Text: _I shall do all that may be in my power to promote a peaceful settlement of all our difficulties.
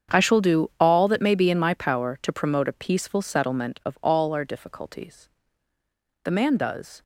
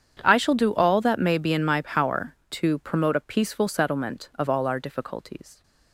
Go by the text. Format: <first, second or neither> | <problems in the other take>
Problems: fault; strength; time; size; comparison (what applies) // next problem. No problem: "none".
second | starts louder than the rest; strong; until 1.2 s; 7.5 dB; strong in the second // goes on to say "The man does"; noticeable; from 6.2 s on; 0.78 s long